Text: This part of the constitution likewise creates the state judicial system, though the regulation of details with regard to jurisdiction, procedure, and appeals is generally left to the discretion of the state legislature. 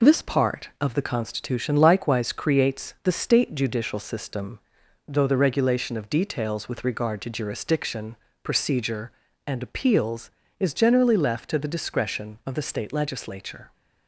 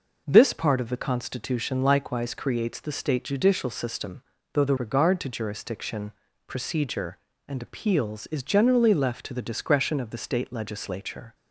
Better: first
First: none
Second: skips "regulation of details with"; at 4.7 s

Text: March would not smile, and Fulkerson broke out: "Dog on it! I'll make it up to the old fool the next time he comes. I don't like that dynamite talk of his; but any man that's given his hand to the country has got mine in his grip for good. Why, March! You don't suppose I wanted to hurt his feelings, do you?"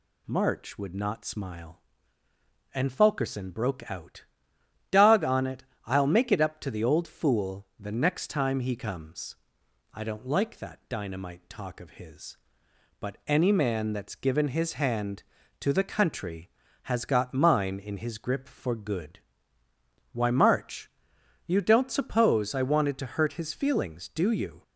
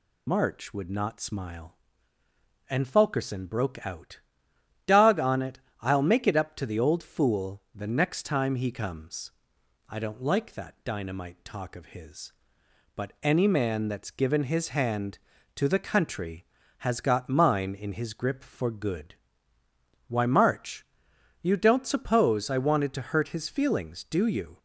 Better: first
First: none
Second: loses the start of "March"; at 0.2 s; 50 ms

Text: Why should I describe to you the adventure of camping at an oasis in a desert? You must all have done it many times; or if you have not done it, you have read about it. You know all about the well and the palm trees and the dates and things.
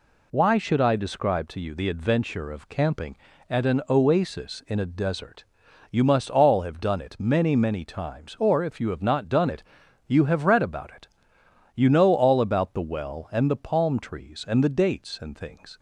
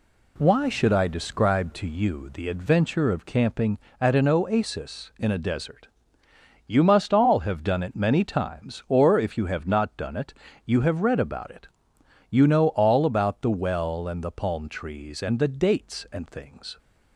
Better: second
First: says "many" twice; at 7.5 s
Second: none

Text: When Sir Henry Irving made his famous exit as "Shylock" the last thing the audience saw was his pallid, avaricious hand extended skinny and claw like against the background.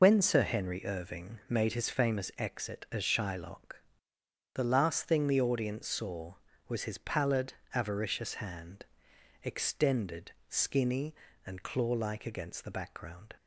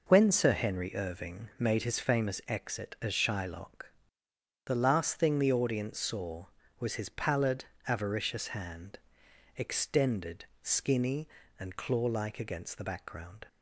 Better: second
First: loses the start of "When"; at 0.0 s; 30 ms // pauses between "Shylock" and "the"; noticeable; at 3.8 s; 0.72 s long // pauses between "hand" and "extended"; noticeable; at 8.8 s; 0.58 s long // pauses between "extended" and "skinny"; slight; at 10.3 s; 0.18 s long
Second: pauses between "Shylock" and "the"; noticeable; at 3.9 s; 0.74 s long // pauses between "hand" and "extended"; noticeable; at 8.9 s; 0.58 s long // pauses between "extended" and "skinny"; slight; at 10.4 s; 0.18 s long

